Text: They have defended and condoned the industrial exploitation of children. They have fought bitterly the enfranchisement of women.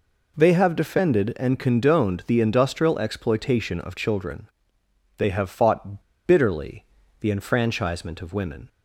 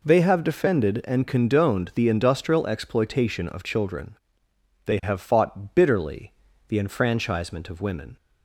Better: second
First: pauses between "fought" and "bitterly"; slight; at 6.0 s; 0.23 s long // pauses between "bitterly" and "the"; slight; at 6.8 s; 0.36 s long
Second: pauses between "bitterly" and "the"; slight; at 6.3 s; 0.36 s long

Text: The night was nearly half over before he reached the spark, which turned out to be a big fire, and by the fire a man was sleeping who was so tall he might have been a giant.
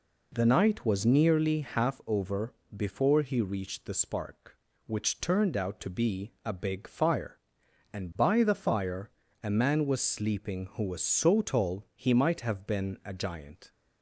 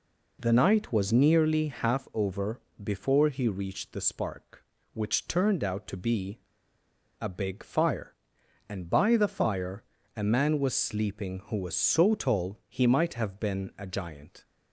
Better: first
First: pauses between "over" and "before"; slight; at 2.5 s; 0.22 s long // pauses between "fire" and "a"; slight; at 9.0 s; 0.32 s long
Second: pauses between "over" and "before"; slight; at 2.5 s; 0.22 s long // pauses between "be" and "a"; noticeable; at 6.3 s; 0.80 s long // pauses between "fire" and "a"; slight; at 9.8 s; 0.32 s long

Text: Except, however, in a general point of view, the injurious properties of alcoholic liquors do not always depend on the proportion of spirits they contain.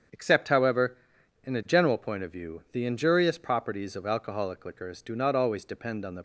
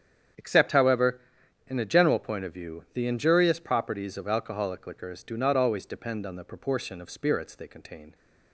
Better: second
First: starts louder than the rest; strong; until 1.6 s; 7.5 dB // stops before "proportion of spirits they contain"; at 6.1 s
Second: starts louder than the rest; strong; until 1.8 s; 8.5 dB

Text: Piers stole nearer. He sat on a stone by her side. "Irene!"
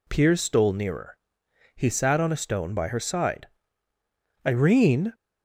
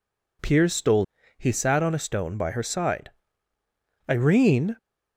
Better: first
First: none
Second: skips "nearer"; at 1.2 s

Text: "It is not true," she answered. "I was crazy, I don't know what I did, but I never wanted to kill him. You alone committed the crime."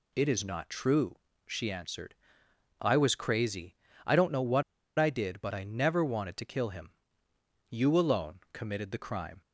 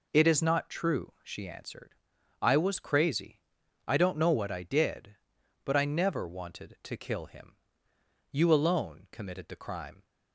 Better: second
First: pauses between "what" and "I"; slight; at 4.6 s; 0.34 s long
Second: none

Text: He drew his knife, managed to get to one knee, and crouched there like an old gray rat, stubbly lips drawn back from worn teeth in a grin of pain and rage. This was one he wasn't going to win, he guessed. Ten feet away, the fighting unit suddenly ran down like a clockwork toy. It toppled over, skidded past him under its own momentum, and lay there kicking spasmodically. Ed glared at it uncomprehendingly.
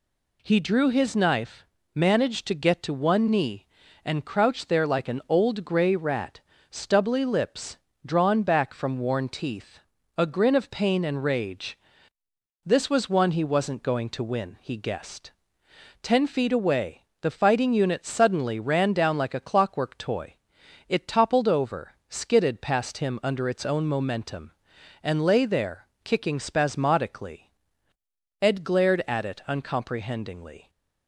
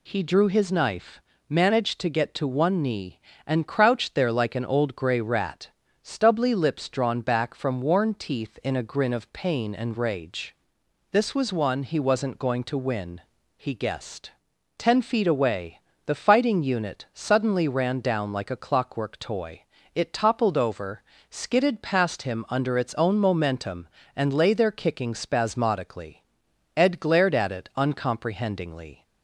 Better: second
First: pauses between "lips" and "drawn"; slight; at 7.7 s; 0.26 s long // skips "in"; at 9.9 s // pauses between "there" and "kicking"; slight; at 25.8 s; 0.18 s long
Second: none

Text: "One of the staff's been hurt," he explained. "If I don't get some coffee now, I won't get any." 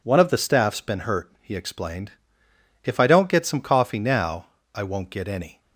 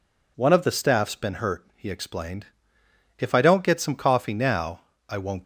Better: first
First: none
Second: stops before "get any"; at 5.4 s

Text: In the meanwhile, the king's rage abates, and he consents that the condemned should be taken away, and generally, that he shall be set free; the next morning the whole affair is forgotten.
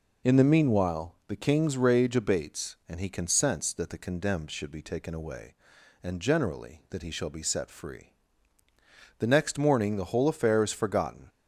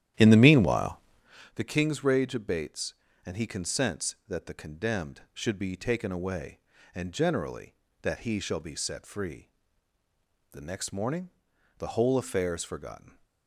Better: first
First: none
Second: starts louder than the rest; strong; until 1.4 s; 11 dB // pauses between "morning" and "the"; noticeable; at 11.3 s; 0.48 s long

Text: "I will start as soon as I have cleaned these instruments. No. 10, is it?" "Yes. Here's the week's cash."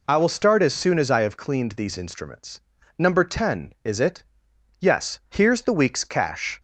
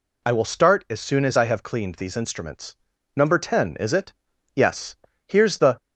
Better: first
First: none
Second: stops before "week's cash"; at 5.7 s

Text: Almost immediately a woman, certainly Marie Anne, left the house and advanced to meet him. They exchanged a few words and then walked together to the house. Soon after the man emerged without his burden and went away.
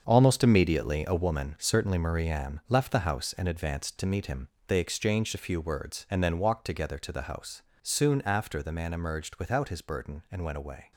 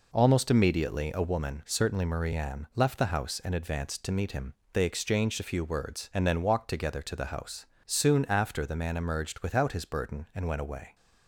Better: second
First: gets quieter; strong; throughout; 10.5 dB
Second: none

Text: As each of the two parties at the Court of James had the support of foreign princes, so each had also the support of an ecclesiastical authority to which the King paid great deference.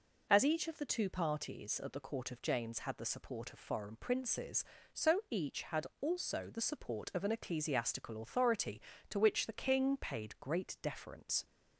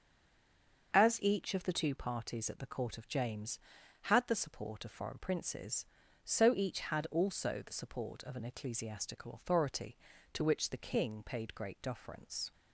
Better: first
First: none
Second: stays silent before the first word; slight; until 0.9 s; 0.9 s long // starts louder than the rest; until 1.9 s; 6.5 dB

